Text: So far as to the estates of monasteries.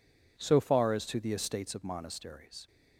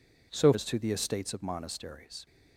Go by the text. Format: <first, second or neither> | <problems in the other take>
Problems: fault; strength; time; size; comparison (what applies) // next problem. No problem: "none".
first | skips "far"; at 0.5 s